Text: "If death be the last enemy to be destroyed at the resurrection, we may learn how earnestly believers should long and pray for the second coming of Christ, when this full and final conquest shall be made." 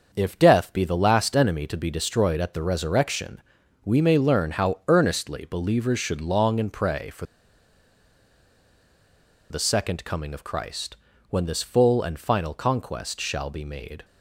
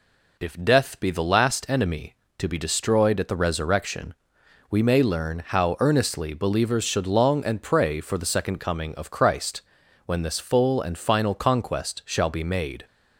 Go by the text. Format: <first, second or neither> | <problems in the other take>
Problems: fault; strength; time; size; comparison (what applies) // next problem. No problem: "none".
second | starts louder than the rest; until 1.1 s; 6.5 dB // pauses between "for" and "the"; strong; at 7.2 s; 2.2 s long